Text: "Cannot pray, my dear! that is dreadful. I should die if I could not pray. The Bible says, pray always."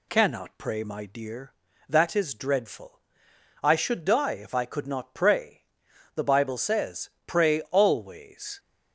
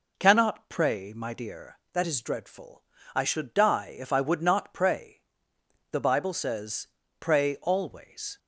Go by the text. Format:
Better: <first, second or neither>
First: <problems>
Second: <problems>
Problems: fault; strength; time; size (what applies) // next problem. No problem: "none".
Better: first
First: none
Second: says "would" for "could"; at 4.1 s